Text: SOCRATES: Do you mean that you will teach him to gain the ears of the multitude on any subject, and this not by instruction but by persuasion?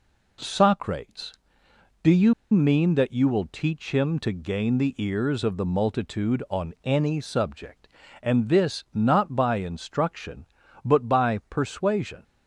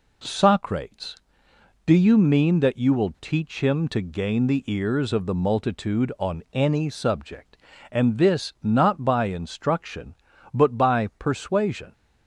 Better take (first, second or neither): second